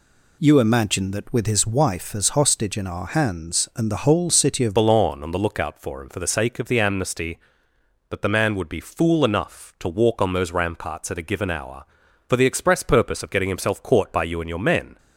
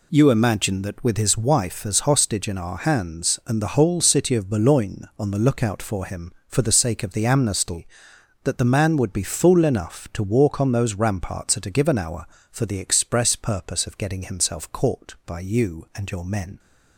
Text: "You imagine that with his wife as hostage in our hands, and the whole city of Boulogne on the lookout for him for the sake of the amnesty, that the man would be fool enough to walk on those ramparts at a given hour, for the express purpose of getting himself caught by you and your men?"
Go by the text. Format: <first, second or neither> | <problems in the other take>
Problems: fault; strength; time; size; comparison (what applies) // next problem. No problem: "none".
second | changes voice at "Boulogne"; from 4.7 s on; 10.2 s long